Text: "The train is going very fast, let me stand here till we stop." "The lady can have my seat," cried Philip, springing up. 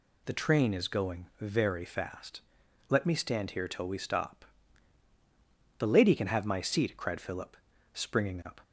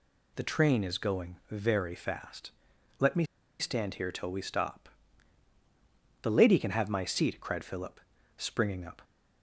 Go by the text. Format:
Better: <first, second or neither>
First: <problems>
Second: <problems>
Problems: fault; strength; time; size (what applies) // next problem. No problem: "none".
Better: first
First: none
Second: pauses between "me" and "stand"; slight; at 3.2 s; 0.33 s long